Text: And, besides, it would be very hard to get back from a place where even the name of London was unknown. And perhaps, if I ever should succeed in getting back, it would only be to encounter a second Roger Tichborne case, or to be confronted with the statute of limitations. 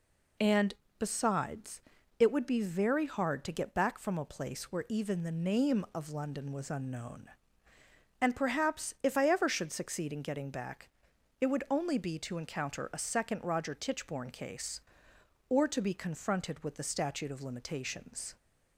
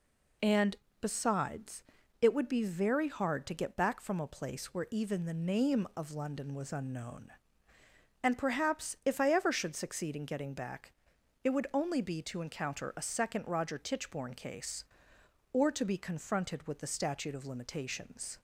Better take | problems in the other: neither | none

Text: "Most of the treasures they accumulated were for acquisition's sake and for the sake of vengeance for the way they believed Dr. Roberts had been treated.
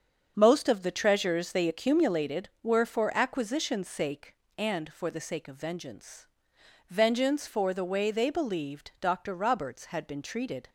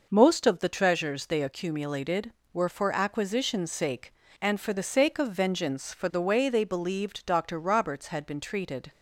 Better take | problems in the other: second | starts louder than the rest; strong; until 1.3 s; 7 dB // says "vengeance" twice; at 6.8 s

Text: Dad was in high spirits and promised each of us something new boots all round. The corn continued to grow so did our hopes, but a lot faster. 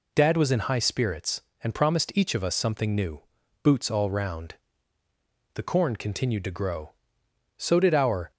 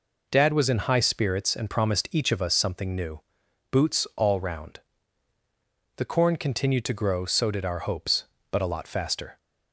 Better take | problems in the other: second | pauses between "new" and "boots"; at 3.2 s; 0.42 s long; noticeable in the second // stops before "hopes but a lot faster"; at 8.3 s

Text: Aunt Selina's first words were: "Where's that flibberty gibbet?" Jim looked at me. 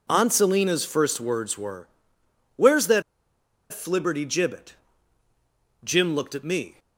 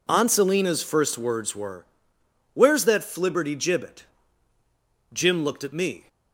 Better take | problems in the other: second | pauses between "that" and "flibberty"; noticeable; at 3.0 s; 0.68 s long

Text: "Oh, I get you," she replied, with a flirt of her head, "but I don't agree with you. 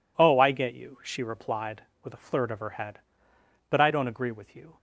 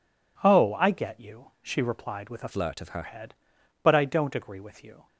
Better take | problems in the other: first | changes voice from "flirt" to "her"; from 2.5 to 3.0 s; 0.5 s long

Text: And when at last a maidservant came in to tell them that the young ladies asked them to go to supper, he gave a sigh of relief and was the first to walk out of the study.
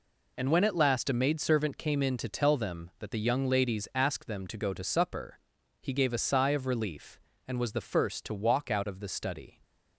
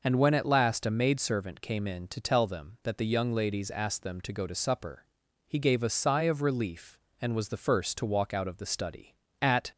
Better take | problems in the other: first | goes on to say "At"; slight; from 9.4 s on; 0.30 s long

